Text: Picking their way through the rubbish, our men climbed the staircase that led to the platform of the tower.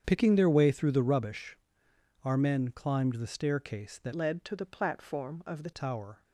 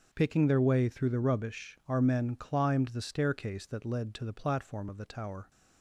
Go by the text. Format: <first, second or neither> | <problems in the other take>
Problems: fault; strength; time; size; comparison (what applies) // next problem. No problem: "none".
second | starts louder than the rest; strong; until 1.0 s; 8 dB; noticeable in the second // changes voice from "led" to "the"; from 4.1 to 5.7 s; 1.6 s long